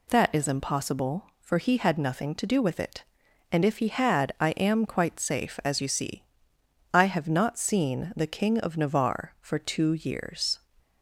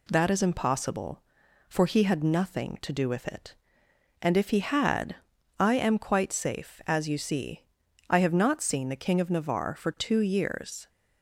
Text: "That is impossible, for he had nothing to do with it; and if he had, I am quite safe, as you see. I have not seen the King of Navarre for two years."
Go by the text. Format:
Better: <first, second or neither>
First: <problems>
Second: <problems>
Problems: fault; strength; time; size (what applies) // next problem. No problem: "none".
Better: neither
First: none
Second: none